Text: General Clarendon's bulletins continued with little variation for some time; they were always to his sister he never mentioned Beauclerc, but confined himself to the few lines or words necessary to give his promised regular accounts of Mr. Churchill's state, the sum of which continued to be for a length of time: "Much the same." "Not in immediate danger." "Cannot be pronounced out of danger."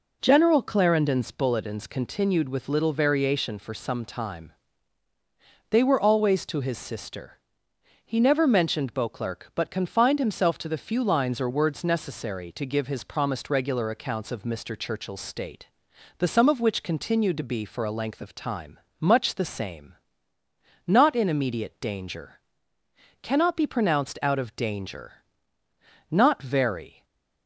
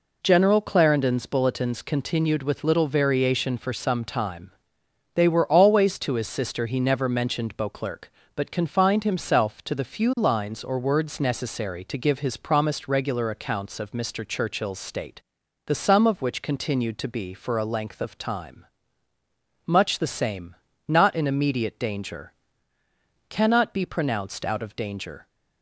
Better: second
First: pauses between "sister" and "he"; noticeable; at 7.3 s; 0.66 s long // goes on to say "Not very"; noticeable; from 26.1 s on; 0.94 s long // stays silent after the last word; slight; from 26.9 s on; 0.5 s long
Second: none

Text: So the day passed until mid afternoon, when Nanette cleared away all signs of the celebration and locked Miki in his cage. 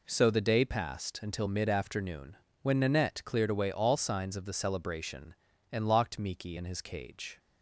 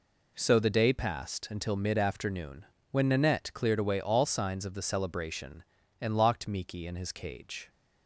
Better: neither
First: none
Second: none

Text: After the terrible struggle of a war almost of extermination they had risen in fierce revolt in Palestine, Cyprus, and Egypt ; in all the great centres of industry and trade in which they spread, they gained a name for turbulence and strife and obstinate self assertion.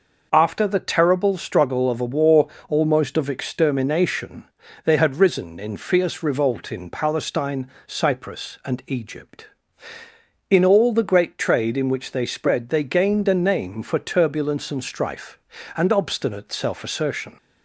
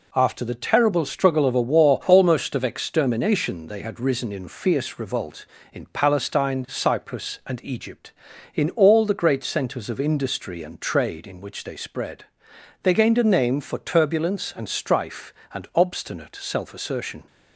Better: second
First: pauses between "war" and "almost"; slight; at 2.4 s; 0.20 s long // pauses between "extermination" and "they"; at 4.4 s; 0.40 s long // skips "centres of industry and"; at 11.3 s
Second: none

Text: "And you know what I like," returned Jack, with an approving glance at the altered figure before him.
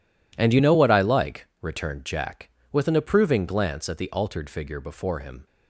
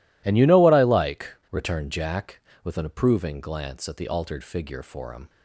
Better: first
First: none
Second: says "for" for "before"; at 4.8 s

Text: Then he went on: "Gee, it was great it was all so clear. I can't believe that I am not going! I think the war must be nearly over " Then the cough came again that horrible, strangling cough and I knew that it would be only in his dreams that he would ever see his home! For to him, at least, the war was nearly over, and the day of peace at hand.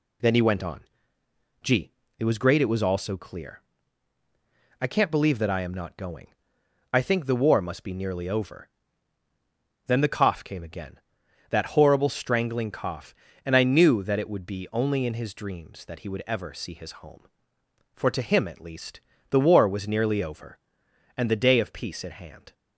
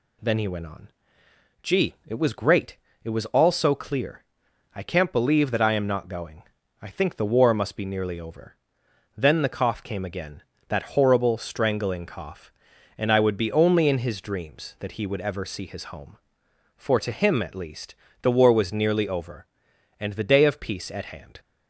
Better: first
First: none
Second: pauses between "great" and "it"; slight; at 2.7 s; 0.28 s long // skips "knew that it"; at 13.2 s

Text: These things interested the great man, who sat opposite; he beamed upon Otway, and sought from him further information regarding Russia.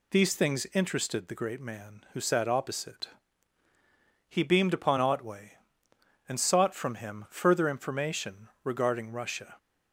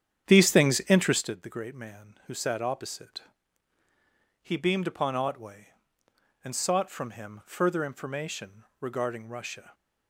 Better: first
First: pauses between "information" and "regarding"; slight; at 8.4 s; 0.15 s long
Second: starts louder than the rest; strong; until 1.3 s; 9 dB // pauses between "information" and "regarding"; slight; at 8.6 s; 0.16 s long

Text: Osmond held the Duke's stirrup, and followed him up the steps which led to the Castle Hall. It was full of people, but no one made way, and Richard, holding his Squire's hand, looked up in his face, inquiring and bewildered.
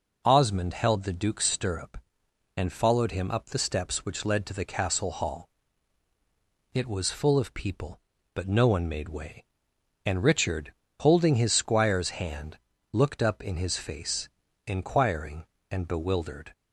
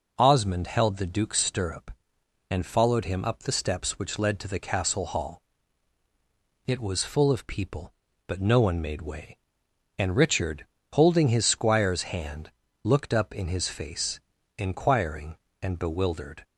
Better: neither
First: none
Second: none

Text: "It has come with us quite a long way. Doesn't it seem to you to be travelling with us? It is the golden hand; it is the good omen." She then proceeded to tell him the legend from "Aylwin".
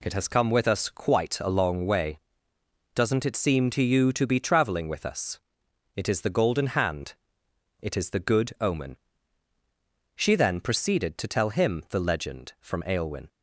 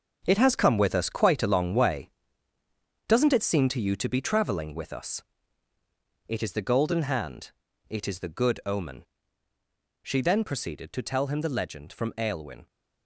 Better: first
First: none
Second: gets quieter; strong; throughout; 10.5 dB

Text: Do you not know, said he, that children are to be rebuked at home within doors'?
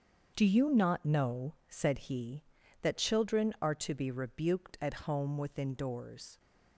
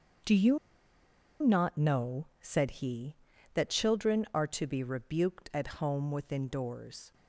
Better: first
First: starts louder than the rest; until 1.3 s; 7 dB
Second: starts louder than the rest; until 2.0 s; 7 dB // pauses between "you" and "not"; noticeable; at 0.5 s; 0.84 s long

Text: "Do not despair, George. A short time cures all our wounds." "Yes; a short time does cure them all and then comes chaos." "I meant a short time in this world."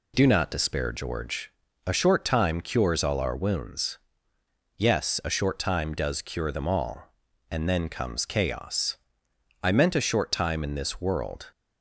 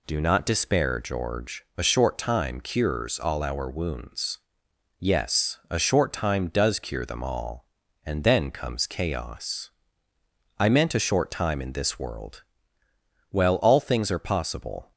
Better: first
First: none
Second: goes on to say "Well all things are possible"; from 13.3 s on; 1.6 s long

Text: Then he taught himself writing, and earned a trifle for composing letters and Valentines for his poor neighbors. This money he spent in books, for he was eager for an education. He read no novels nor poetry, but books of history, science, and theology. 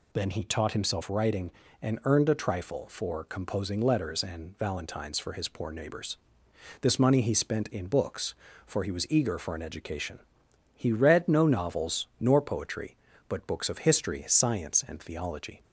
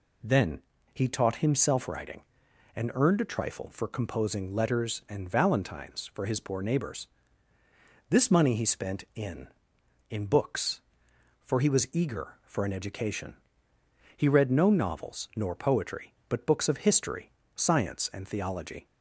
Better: first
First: none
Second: pauses between "Then" and "he"; slight; at 0.5 s; 0.34 s long // says "in" twice; at 10.0 s

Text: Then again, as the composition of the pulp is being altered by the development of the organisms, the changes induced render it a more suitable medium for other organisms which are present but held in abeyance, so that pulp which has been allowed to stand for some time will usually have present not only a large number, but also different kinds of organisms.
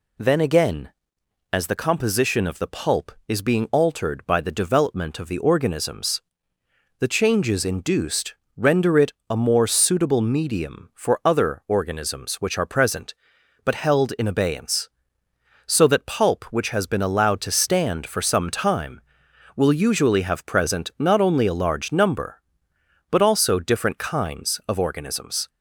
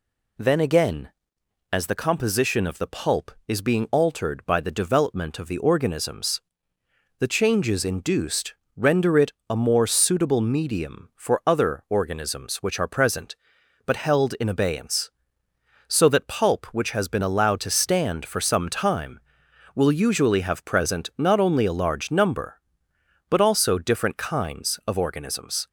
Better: neither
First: pauses between "induced" and "render"; slight; at 8.3 s; 0.22 s long // pauses between "it" and "a"; slight; at 9.1 s; 0.16 s long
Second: pauses between "induced" and "render"; slight; at 8.5 s; 0.22 s long // pauses between "it" and "a"; slight; at 9.3 s; 0.16 s long

